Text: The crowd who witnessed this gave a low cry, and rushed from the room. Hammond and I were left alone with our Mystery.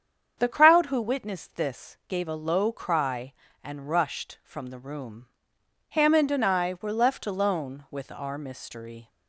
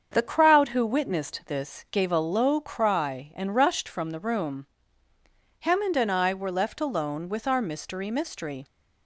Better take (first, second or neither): first